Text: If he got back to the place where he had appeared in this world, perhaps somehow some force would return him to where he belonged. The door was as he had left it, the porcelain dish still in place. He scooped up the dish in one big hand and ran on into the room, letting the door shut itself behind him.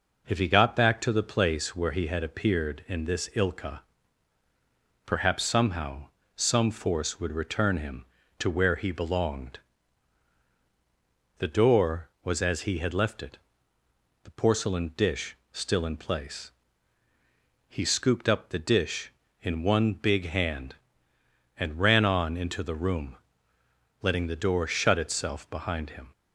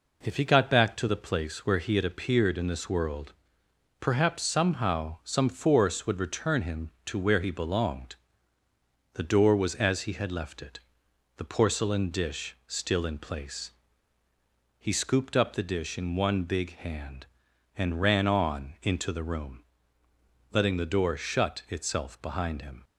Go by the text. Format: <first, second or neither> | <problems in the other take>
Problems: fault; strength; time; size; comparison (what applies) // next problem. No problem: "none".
second | says "ilka" for "world"; at 3.3 s // pauses between "somehow" and "some"; slight; at 6.0 s; 0.28 s long // pauses between "dish" and "still"; slight; at 15.3 s; 0.16 s long